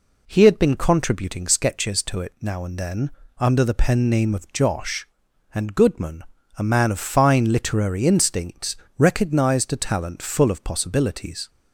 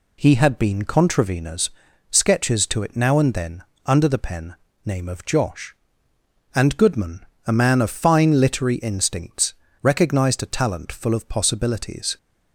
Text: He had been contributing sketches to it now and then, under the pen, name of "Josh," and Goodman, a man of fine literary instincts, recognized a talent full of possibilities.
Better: first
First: none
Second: says "contraveners" for "contributing"; at 0.8 s

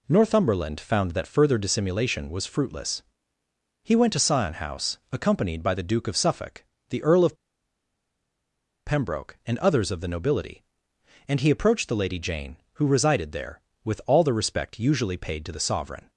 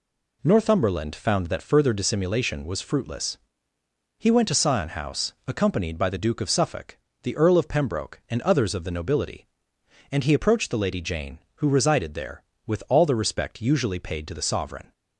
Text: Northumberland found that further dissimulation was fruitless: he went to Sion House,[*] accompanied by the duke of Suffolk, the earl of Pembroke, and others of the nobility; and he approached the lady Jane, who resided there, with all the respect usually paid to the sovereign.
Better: second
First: pauses between "of" and "Pembroke"; strong; at 7.3 s; 1.5 s long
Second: none

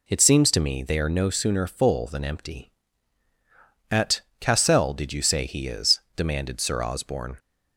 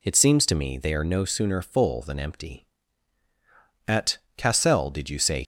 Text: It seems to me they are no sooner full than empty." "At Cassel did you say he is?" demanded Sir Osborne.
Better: first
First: pauses between "At" and "Cassel"; slight; at 4.2 s; 0.18 s long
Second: pauses between "At" and "Cassel"; slight; at 4.1 s; 0.18 s long // stops before "he is demanded Sir Osborne"; at 5.4 s

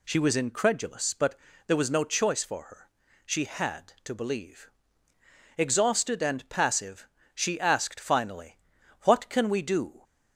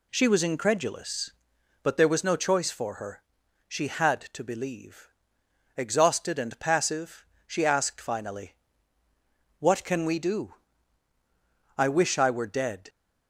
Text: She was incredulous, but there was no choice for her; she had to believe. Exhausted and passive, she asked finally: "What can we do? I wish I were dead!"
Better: second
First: pauses between "but" and "there"; slight; at 1.3 s; 0.30 s long // stops before "I wish I were dead"; at 10.0 s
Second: none

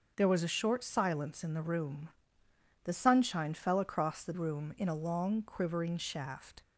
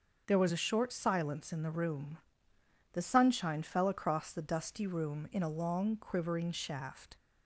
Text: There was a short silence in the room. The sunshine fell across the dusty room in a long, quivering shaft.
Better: second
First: starts louder than the rest; noticeable; until 1.1 s; 6 dB // skips "dusty"; at 4.3 s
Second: starts louder than the rest; noticeable; until 1.2 s; 6 dB

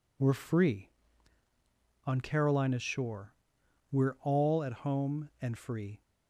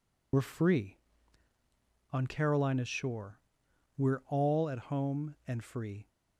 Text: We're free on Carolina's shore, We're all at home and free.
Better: first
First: none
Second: loses the start of "We're"; at 0.3 s; 60 ms

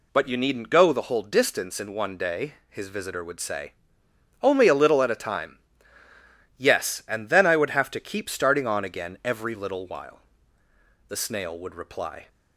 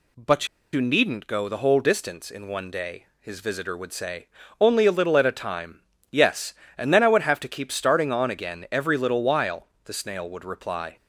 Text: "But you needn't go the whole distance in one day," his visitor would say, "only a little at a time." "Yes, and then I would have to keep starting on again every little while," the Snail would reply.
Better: first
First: none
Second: pauses between "But" and "you"; slight; at 0.4 s; 0.26 s long

